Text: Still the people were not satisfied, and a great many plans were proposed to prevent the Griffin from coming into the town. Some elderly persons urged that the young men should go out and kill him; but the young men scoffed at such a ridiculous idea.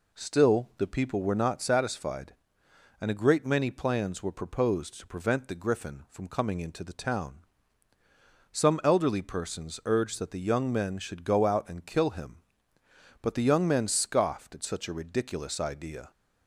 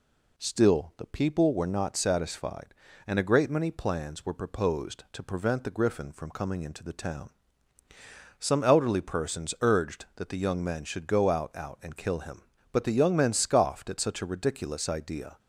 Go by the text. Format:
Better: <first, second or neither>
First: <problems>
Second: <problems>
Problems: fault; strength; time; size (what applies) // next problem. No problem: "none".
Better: first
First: none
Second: says "out" twice; at 11.5 s